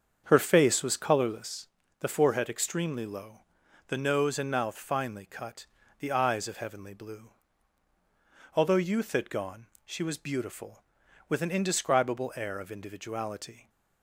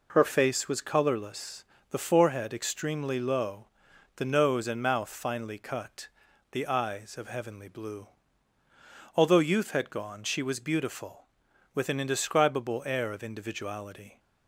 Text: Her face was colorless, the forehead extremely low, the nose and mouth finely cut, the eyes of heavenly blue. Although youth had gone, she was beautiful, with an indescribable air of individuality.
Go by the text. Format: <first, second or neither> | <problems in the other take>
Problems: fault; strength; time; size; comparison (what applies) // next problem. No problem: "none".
second | starts louder than the rest; strong; until 1.7 s; 7 dB